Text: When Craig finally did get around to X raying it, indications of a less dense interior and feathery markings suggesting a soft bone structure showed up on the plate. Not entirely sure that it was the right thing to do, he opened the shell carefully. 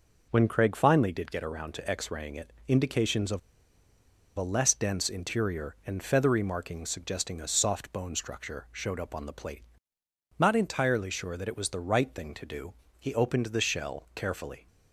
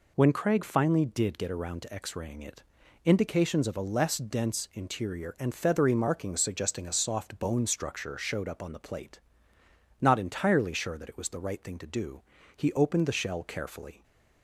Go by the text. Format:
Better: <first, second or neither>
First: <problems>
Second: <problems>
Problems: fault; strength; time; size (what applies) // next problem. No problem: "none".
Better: second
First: pauses between "of" and "a"; noticeable; at 3.3 s; 0.96 s long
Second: none